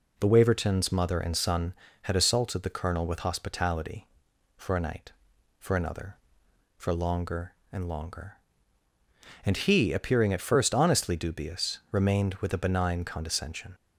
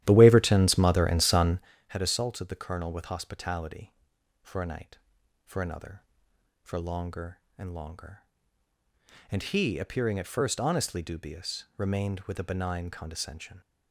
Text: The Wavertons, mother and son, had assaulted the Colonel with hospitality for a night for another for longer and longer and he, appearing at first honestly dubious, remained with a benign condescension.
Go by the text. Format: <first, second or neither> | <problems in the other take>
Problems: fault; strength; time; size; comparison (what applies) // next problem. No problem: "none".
first | starts louder than the rest; strong; until 1.7 s; 13 dB